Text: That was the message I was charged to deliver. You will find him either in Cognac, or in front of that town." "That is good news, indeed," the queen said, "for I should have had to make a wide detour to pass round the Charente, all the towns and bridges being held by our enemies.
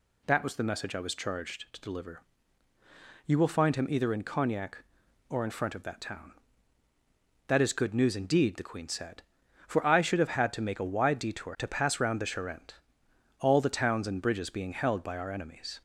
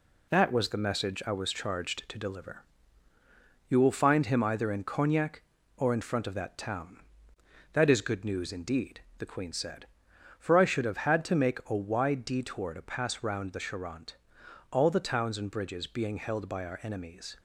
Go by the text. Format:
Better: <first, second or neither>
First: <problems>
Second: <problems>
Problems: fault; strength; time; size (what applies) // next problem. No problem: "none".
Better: first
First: none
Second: gets quieter; noticeable; throughout; 4.5 dB